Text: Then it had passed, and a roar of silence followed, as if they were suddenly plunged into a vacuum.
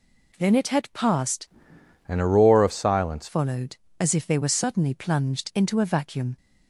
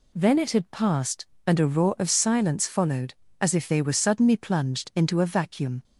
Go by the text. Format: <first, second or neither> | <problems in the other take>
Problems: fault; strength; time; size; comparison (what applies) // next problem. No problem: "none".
second | changes voice from "and" to "silence"; from 2.0 to 3.2 s; 1.2 s long